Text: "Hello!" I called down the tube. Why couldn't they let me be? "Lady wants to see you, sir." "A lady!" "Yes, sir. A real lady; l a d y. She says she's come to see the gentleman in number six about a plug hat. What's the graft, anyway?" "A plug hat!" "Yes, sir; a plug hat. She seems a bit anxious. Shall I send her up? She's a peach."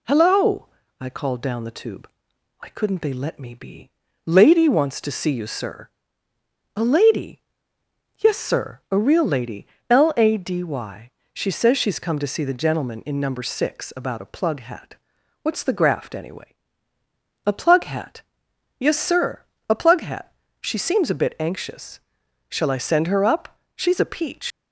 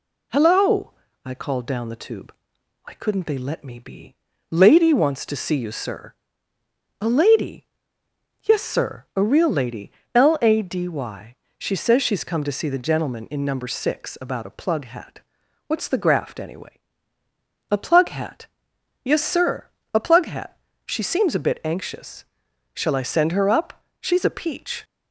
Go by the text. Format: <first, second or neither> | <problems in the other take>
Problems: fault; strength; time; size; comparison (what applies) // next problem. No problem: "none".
second | leaves "peach" unfinished; at 24.5 s; 85 ms